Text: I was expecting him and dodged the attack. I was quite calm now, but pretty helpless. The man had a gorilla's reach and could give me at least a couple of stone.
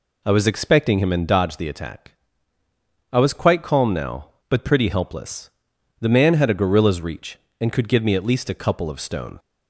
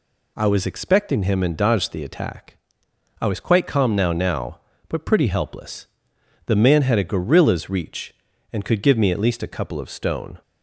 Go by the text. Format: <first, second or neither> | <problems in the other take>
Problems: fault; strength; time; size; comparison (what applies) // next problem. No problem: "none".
first | says "now" twice; at 4.1 s